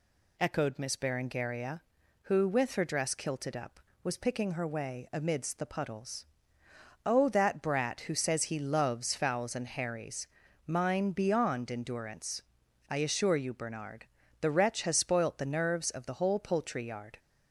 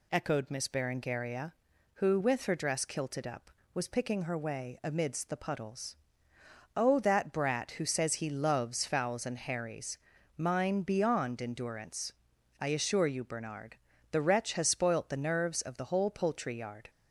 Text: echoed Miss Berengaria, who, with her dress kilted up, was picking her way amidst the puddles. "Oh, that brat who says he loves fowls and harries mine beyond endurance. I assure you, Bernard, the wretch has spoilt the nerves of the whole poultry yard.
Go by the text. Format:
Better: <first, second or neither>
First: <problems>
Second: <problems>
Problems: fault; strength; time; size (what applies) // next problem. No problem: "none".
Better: neither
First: pauses between "harries" and "mine"; at 10.2 s; 0.42 s long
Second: pauses between "harries" and "mine"; at 9.9 s; 0.42 s long